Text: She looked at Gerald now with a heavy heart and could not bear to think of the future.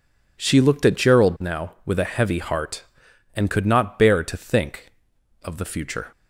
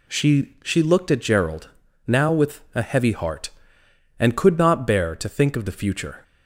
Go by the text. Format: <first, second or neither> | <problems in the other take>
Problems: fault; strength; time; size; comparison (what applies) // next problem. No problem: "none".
first | says "She" twice; at 0.6 s // pauses between "Gerald" and "now"; at 1.6 s; 0.38 s long